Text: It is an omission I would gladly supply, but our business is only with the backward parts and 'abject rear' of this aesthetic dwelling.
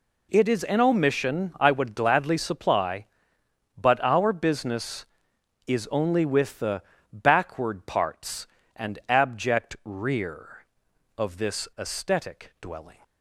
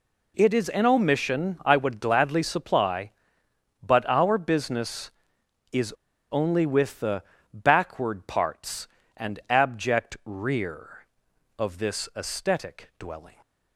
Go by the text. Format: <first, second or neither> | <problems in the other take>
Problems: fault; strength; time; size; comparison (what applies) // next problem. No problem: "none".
first | pauses between "is" and "only"; at 5.9 s; 0.37 s long // pauses between "the" and "backward"; slight; at 7.2 s; 0.30 s long; slight in the first